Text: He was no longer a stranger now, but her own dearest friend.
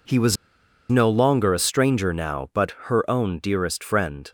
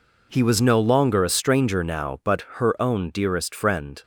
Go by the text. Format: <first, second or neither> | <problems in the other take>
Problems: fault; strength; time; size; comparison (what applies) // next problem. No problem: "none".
second | pauses between "was" and "no"; noticeable; at 0.3 s; 0.54 s long // pauses between "but" and "her"; slight; at 2.7 s; 0.16 s long; slight in the second